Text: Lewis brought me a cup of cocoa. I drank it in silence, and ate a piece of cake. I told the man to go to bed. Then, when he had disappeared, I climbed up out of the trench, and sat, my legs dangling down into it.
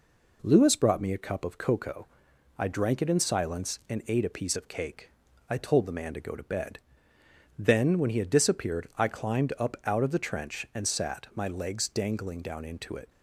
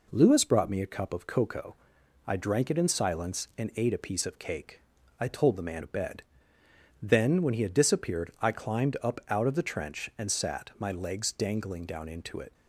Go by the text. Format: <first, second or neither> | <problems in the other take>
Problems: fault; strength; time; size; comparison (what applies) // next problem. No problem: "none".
first | skips "to go"; at 5.8 s